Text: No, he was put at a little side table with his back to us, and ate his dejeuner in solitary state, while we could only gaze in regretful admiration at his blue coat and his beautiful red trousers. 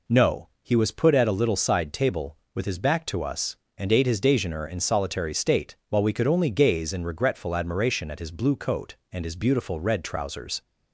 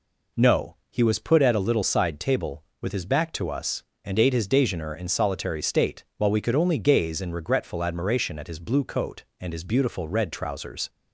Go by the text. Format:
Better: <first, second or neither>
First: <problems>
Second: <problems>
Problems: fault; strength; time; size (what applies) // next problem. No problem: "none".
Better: neither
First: none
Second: none